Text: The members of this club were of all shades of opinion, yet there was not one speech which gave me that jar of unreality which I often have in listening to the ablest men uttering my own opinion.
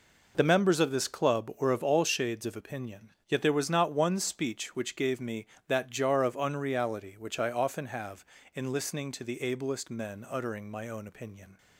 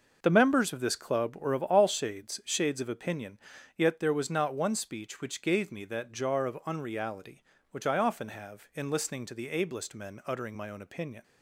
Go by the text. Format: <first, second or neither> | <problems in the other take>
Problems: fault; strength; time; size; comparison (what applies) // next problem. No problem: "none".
first | says "shades" twice; at 2.4 s